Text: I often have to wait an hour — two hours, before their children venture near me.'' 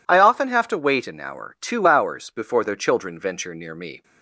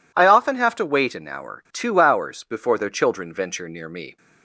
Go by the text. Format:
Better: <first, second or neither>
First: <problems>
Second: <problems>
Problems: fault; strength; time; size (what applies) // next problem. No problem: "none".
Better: neither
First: none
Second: none